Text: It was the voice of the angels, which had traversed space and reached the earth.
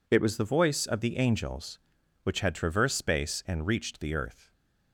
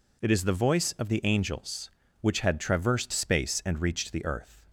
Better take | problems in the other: first | says "is" for "was"; at 0.3 s

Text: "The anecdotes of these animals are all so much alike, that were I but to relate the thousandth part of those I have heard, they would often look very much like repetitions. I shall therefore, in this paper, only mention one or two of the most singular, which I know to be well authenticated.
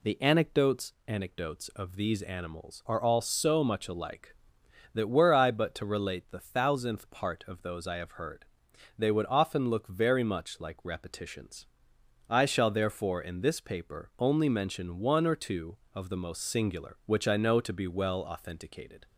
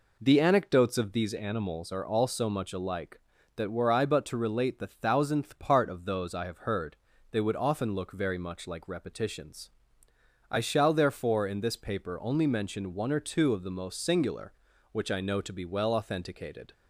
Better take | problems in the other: second | says "anecdotes" twice; at 1.0 s

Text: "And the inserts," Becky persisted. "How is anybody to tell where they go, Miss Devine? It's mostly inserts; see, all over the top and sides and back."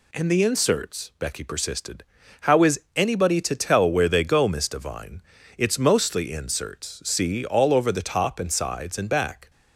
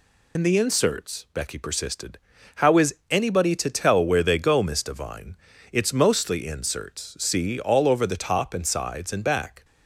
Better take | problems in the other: first | loses the start of "And"; at 0.3 s; 75 ms // pauses between "is" and "anybody"; slight; at 2.9 s; 0.16 s long; slight in the first

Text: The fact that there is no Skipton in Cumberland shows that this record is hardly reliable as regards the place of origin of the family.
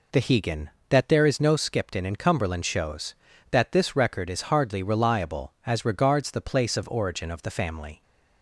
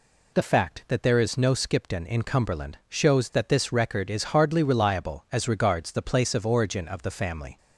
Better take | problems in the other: second | says "hegan" for "fact"; at 0.2 s

